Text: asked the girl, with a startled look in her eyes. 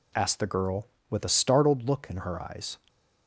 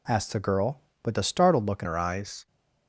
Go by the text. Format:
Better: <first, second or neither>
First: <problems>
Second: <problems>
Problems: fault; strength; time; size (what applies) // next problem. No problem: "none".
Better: first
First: none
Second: changes voice at "her"; from 1.8 s on; 0.6 s long